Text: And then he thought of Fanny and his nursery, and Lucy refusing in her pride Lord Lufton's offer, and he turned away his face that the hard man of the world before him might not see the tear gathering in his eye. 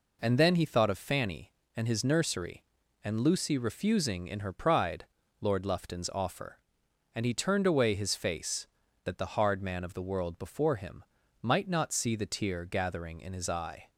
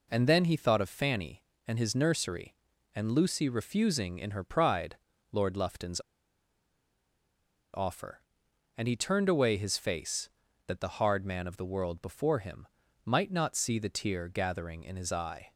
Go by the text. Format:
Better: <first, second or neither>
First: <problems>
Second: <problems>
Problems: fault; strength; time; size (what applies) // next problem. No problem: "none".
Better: first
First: pauses between "pride" and "Lord"; slight; at 5.0 s; 0.36 s long // pauses between "him" and "might"; at 11.0 s; 0.38 s long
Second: pauses between "pride" and "Lord"; slight; at 4.9 s; 0.36 s long // pauses between "Lufton's" and "offer"; strong; at 6.0 s; 1.7 s long // pauses between "him" and "might"; at 12.6 s; 0.38 s long